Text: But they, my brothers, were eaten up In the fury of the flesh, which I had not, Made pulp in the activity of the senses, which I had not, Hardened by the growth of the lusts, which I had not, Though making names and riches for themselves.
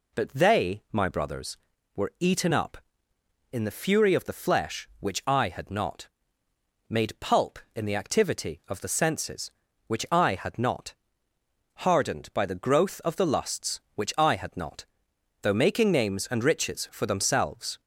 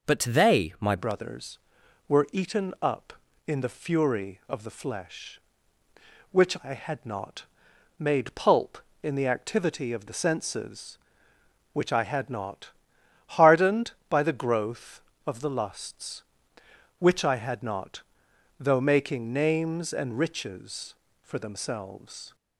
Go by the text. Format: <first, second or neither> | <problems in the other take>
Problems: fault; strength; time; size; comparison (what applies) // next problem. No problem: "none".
first | changes voice at "brothers"; from 0.9 s on; 21.4 s long